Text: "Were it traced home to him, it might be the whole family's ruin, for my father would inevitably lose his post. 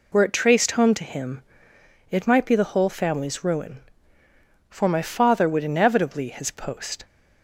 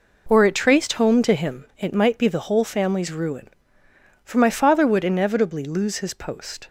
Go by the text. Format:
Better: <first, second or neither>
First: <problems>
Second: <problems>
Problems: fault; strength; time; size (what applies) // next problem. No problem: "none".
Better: second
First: skips "lose"; at 6.2 s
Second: none